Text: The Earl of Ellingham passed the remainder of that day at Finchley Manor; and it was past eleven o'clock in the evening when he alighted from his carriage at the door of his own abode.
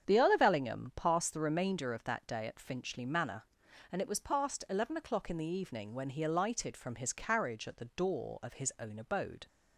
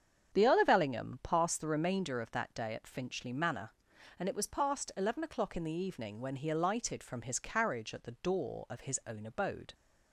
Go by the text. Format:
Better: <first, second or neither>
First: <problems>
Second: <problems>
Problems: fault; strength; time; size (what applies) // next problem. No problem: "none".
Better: neither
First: starts louder than the rest; strong; until 1.1 s; 8 dB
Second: starts louder than the rest; strong; until 1.3 s; 8 dB